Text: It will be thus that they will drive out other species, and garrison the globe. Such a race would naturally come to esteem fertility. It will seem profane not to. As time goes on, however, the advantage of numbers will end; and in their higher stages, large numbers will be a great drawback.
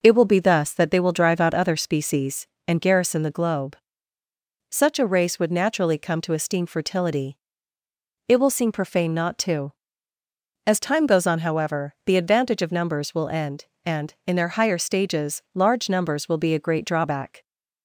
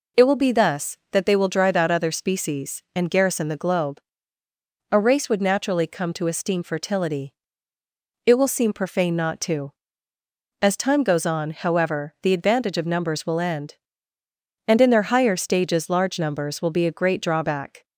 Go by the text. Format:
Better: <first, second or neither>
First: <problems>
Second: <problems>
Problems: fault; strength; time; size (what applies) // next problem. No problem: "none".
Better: first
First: none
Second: skips "Such"; at 4.4 s